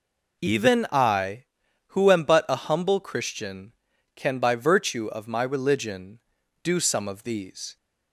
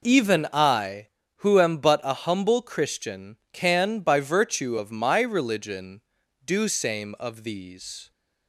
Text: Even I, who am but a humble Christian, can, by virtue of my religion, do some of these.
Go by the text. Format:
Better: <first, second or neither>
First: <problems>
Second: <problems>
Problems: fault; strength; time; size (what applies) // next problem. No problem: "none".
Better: first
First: none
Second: says "same" for "some"; at 6.6 s